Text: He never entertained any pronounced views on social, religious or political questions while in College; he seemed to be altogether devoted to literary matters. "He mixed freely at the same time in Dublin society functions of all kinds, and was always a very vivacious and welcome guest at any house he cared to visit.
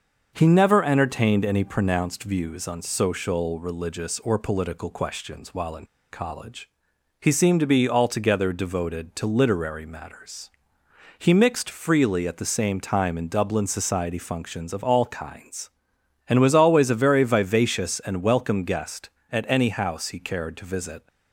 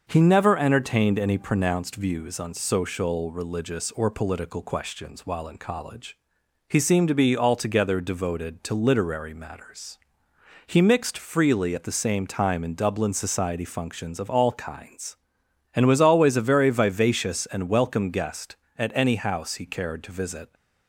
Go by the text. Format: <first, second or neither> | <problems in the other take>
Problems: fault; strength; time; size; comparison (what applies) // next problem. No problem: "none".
second | starts louder than the rest; until 1.3 s; 6.5 dB; also in the second // pauses between "in" and "College"; slight; at 5.8 s; 0.26 s long